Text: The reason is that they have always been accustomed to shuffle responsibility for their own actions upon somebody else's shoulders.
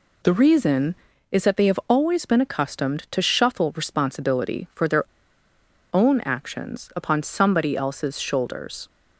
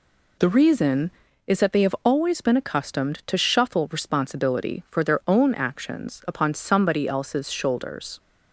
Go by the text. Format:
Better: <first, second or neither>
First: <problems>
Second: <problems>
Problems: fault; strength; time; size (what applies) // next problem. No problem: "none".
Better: second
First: pauses between "their" and "own"; noticeable; at 5.0 s; 0.87 s long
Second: none